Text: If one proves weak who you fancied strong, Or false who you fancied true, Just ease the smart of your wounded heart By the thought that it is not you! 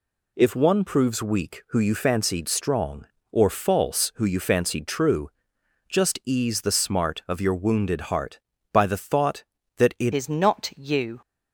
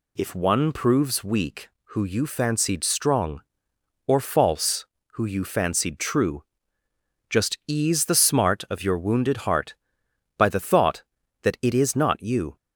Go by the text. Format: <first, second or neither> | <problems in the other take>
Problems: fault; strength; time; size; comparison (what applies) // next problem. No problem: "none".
second | changes voice at "is"; from 10.1 s on; 1.0 s long